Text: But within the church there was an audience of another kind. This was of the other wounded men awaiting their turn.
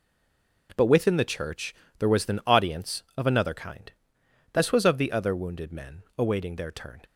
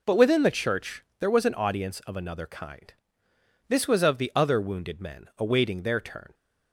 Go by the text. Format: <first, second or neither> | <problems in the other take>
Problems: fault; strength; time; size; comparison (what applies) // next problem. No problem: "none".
second | stays silent before the first word; slight; until 0.6 s; 0.6 s long // pauses between "church" and "there"; slight; at 1.7 s; 0.24 s long; slight in the second